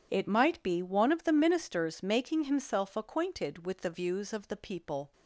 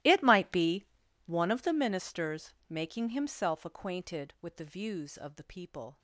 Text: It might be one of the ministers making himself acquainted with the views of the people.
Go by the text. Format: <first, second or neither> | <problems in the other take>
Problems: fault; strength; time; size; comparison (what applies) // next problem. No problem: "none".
first | gets quieter; strong; throughout; 20.5 dB // pauses between "be" and "one"; at 0.8 s; 0.40 s long // pauses between "ministers" and "making"; slight; at 2.5 s; 0.16 s long